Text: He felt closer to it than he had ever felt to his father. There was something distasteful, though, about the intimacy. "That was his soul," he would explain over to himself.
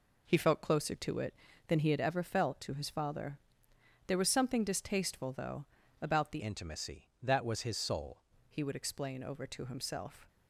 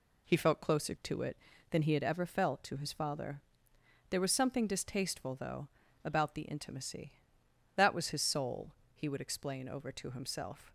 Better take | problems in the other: second | changes voice from "intimacy" to "soul"; from 6.4 to 8.2 s; 1.8 s long

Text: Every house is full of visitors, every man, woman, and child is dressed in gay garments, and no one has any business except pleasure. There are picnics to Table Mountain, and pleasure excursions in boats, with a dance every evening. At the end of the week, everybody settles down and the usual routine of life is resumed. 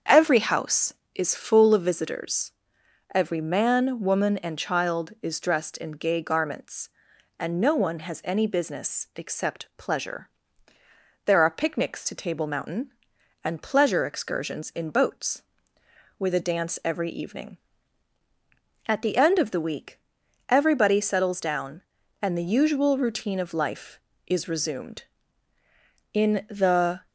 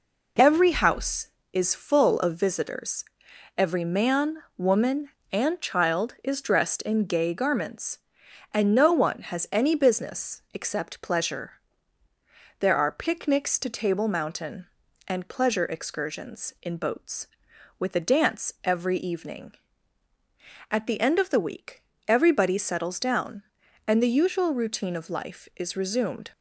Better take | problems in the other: second | starts louder than the rest; strong; until 1.2 s; 7.5 dB // goes on to say "In the"; noticeable; from 26.1 s on; 0.94 s long

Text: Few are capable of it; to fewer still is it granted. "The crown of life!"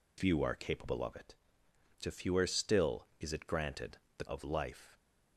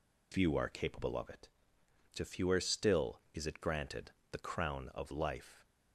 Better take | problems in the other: second | skips "crown"; at 4.2 s

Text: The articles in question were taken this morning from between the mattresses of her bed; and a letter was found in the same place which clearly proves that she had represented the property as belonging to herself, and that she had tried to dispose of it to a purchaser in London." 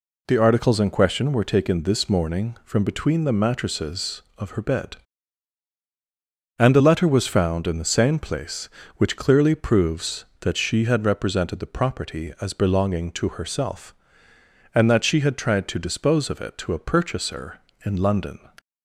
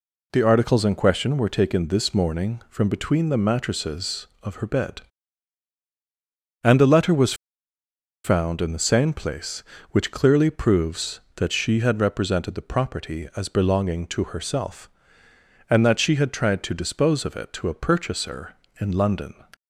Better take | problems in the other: first | pauses between "was" and "found"; noticeable; at 7.3 s; 0.90 s long

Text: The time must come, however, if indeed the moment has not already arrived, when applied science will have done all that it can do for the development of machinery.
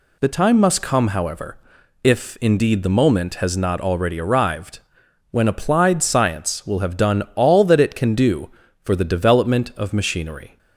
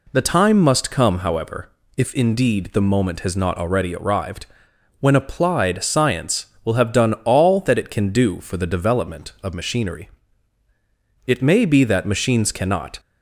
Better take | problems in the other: first | goes on to say "It may be that machines cannot"; strong; from 11.2 s on; 1.7 s long

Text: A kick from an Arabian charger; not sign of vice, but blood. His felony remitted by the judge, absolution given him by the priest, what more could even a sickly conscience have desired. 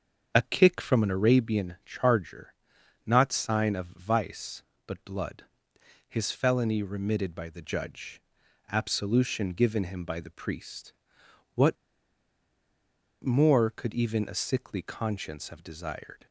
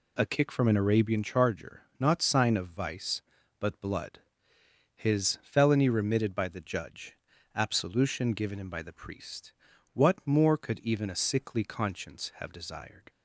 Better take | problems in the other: second | starts louder than the rest; until 1.3 s; 7 dB // pauses between "what" and "more"; strong; at 11.7 s; 1.4 s long

